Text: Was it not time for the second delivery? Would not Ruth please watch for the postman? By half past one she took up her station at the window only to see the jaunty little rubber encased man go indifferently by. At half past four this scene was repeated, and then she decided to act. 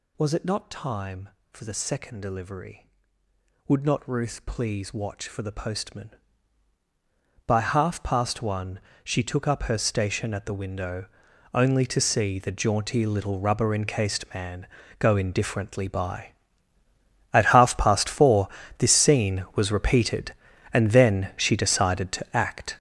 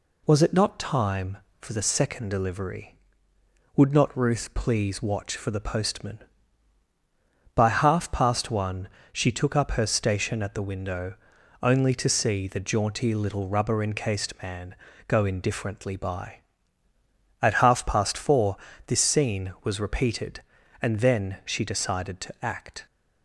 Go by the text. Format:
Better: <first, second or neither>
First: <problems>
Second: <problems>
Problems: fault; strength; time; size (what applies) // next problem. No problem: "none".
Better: second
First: gets louder; strong; throughout; 11.5 dB // pauses between "one" and "she"; slight; at 8.7 s; 0.24 s long // pauses between "window" and "only"; noticeable; at 11.0 s; 0.48 s long // pauses between "man" and "go"; slight; at 14.6 s; 0.32 s long // pauses between "four" and "this"; slight; at 18.4 s; 0.30 s long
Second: pauses between "one" and "she"; slight; at 8.8 s; 0.24 s long // pauses between "window" and "only"; noticeable; at 11.1 s; 0.48 s long // pauses between "man" and "go"; slight; at 14.7 s; 0.32 s long // pauses between "four" and "this"; slight; at 18.5 s; 0.30 s long